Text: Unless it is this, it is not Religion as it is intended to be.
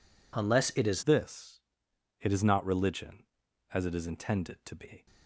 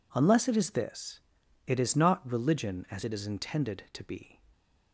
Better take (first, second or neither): second